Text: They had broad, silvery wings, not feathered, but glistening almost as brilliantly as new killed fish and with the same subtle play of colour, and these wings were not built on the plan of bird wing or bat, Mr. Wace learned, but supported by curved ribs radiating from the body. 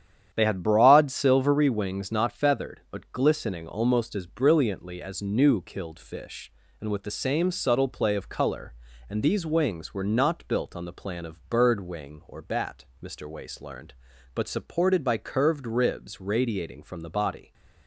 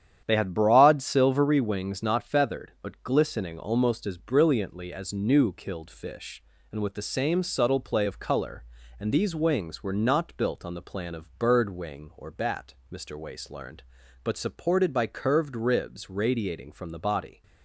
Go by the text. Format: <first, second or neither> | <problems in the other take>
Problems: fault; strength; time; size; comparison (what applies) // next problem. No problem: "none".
neither | starts louder than the rest; strong; the same in both